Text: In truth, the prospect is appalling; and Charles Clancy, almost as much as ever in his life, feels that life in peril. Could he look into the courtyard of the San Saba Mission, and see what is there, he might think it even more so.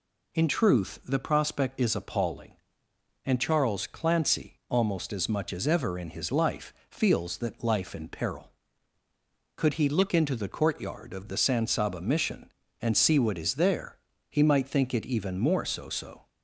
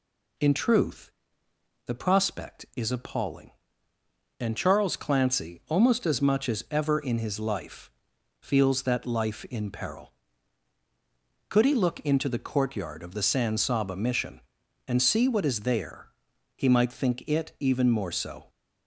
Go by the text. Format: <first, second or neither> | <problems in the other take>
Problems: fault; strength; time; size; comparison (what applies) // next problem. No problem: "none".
second | says "so" twice; at 15.8 s